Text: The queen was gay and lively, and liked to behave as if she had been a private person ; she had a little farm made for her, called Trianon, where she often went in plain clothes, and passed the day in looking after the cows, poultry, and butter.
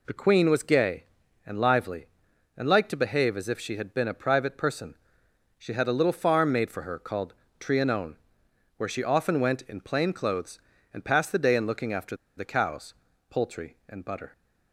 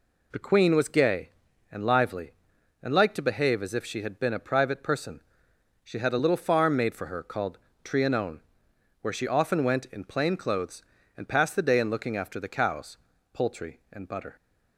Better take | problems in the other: second | pauses between "called" and "Trianon"; slight; at 7.3 s; 0.26 s long; slight in the second // pauses between "after" and "the"; slight; at 12.1 s; 0.23 s long

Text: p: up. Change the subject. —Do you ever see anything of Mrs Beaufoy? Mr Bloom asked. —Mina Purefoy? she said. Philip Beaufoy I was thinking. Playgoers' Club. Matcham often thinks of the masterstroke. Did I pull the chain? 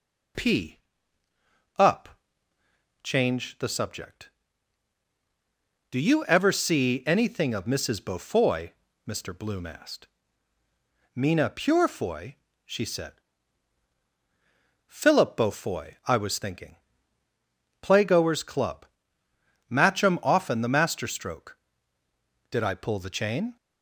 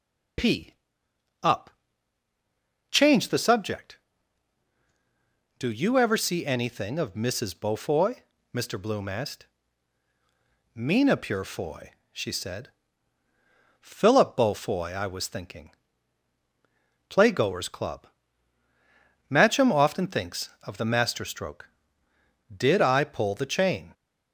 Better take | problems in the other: second | skips "thinks of"; at 20.6 s

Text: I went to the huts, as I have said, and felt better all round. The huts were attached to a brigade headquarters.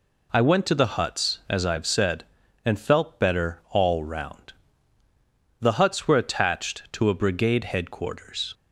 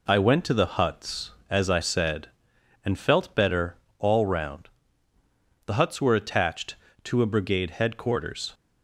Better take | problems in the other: first | skips "have"; at 1.8 s // pauses between "better" and "all"; slight; at 3.7 s; 0.22 s long

